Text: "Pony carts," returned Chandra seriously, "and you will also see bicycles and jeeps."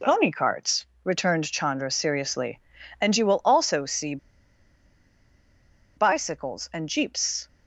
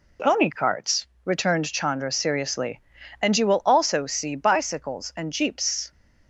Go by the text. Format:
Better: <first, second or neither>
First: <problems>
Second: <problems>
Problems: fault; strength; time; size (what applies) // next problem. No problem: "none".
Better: second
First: pauses between "see" and "bicycles"; strong; at 4.1 s; 1.8 s long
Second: none